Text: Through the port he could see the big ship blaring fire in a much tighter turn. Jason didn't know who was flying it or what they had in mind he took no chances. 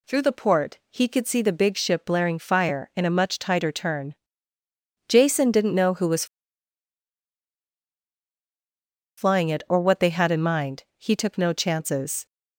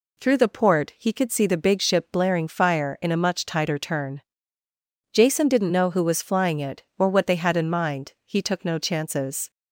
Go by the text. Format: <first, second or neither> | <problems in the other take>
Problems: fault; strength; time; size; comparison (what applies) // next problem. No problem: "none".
second | pauses between "was" and "flying"; strong; at 6.2 s; 2.9 s long